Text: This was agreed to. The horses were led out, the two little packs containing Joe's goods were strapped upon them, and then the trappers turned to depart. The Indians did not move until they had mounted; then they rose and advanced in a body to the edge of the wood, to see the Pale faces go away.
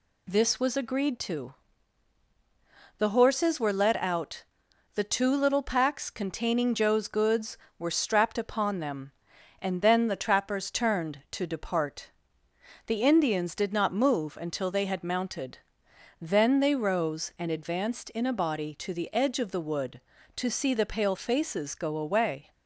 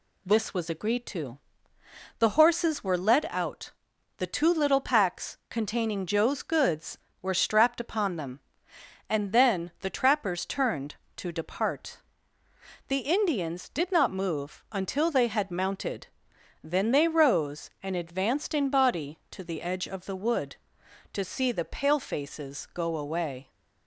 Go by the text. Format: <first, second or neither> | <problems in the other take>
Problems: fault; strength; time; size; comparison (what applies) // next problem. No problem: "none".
first | skips "a"; at 18.6 s